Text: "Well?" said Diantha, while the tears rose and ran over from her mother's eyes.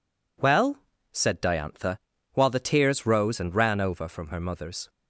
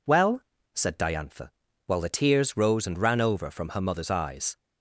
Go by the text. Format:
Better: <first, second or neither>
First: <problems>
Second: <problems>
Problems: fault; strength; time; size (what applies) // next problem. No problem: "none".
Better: second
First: stops before "eyes"; at 4.8 s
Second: none